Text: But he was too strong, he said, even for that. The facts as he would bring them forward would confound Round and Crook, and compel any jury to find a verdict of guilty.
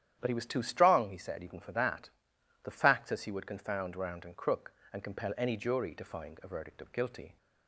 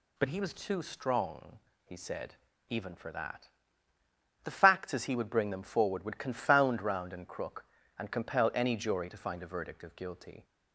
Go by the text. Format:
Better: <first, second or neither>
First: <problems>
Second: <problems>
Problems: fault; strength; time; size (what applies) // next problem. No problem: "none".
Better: second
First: starts louder than the rest; strong; until 1.2 s; 10.5 dB // skips "would bring them forward"; at 3.3 s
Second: none